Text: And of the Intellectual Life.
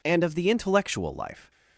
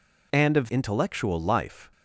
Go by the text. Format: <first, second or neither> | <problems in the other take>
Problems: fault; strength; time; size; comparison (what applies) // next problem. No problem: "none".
first | skips "the"; at 0.6 s